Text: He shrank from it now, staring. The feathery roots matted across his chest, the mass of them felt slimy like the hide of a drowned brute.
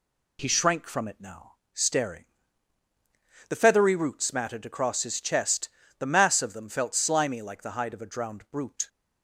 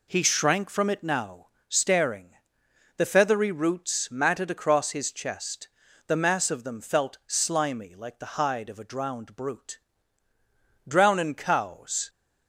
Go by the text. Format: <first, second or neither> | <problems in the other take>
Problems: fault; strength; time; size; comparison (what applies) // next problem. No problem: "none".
first | goes on to say "Drownin cows"; noticeable; from 10.8 s on; 1.2 s long